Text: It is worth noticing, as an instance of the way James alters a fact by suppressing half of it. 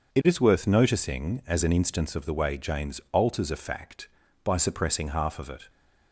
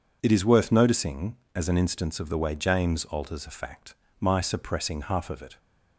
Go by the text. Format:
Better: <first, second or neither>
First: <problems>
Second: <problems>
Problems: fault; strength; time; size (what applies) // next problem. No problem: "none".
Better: first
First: none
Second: says "my" for "by"; at 4.1 s